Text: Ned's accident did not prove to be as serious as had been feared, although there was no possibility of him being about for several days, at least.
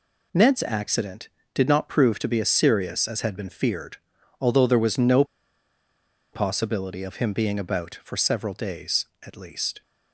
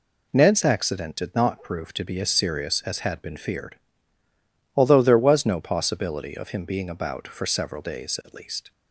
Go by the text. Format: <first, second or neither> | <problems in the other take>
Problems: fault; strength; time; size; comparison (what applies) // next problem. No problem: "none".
second | pauses between "no" and "possibility"; at 5.2 s; 1.0 s long